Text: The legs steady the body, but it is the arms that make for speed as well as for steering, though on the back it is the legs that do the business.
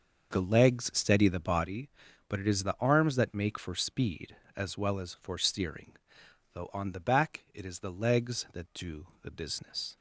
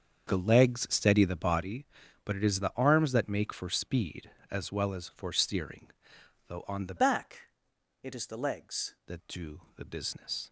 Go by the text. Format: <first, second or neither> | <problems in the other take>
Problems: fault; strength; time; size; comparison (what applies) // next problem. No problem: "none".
first | starts louder than the rest; strong; until 1.3 s; 7 dB; also in the first // changes voice from "back" to "legs"; from 6.9 to 8.9 s; 2.0 s long // pauses between "back" and "it"; noticeable; at 7.4 s; 0.54 s long // pauses between "do" and "the"; slight; at 9.5 s; 0.16 s long; slight in the first